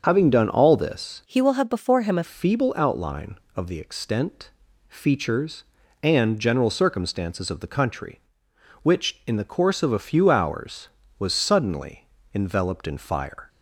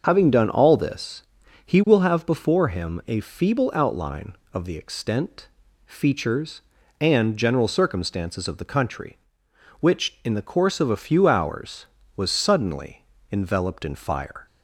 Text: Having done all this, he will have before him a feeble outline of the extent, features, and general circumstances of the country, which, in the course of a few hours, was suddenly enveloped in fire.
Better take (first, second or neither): second